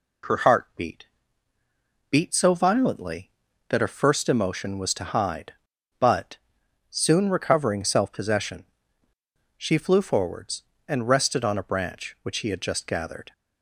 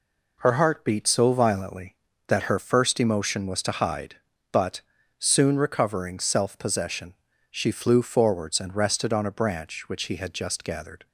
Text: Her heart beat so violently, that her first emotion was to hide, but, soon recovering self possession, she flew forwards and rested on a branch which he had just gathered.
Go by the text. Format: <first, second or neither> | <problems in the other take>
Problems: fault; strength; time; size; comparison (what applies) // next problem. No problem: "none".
second | says "beat" twice; at 2.1 s